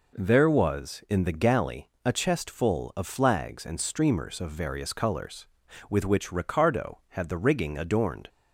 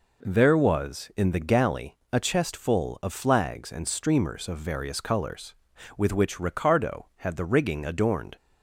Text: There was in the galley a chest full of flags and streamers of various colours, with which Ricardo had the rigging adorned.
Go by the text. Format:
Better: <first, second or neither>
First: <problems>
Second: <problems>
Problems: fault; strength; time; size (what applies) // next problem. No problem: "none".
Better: neither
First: pauses between "galley" and "a"; slight; at 1.8 s; 0.18 s long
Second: pauses between "galley" and "a"; slight; at 1.9 s; 0.18 s long